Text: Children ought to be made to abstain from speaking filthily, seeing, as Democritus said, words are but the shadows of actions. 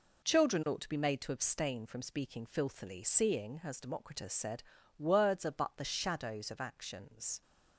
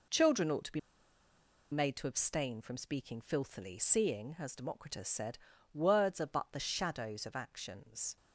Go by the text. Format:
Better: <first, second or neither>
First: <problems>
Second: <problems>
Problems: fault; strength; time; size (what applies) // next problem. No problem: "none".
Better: first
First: none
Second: pauses between "be" and "made"; noticeable; at 0.7 s; 0.92 s long